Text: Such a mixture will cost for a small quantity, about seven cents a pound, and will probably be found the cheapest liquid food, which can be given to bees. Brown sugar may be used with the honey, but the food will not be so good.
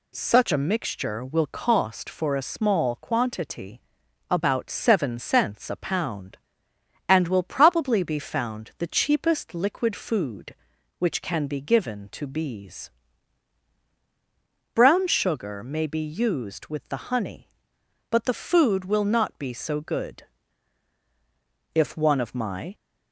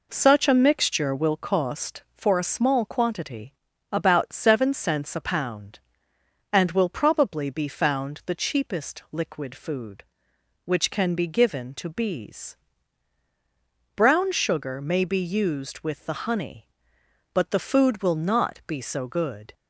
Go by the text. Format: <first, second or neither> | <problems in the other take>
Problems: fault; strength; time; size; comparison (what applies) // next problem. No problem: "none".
second | goes on to say "If one of my"; noticeable; from 21.7 s on; 1.0 s long